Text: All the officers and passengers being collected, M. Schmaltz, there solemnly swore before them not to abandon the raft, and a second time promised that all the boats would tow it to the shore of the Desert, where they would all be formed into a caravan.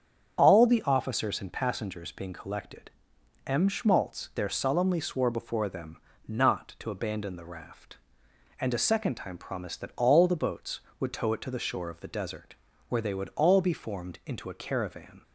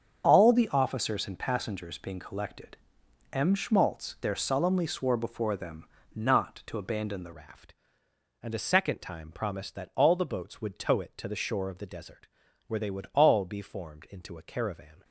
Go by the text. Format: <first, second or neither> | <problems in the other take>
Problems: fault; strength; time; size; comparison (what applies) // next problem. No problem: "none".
first | starts louder than the rest; strong; until 1.2 s; 7.5 dB; strong in the first // pauses between "them" and "not"; slight; at 5.8 s; 0.30 s long; slight in the first // changes voice at "raft"; from 7.3 s on; 7.7 s long